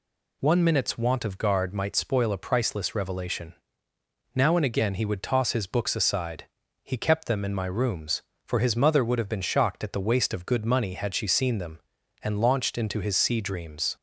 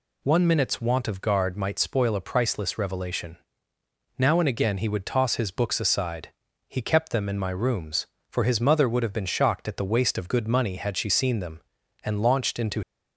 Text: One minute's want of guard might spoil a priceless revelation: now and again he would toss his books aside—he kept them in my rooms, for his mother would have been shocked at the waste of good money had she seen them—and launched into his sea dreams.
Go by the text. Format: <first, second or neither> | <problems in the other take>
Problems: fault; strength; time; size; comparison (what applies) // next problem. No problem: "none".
first | stops before "his sea dreams"; at 12.8 s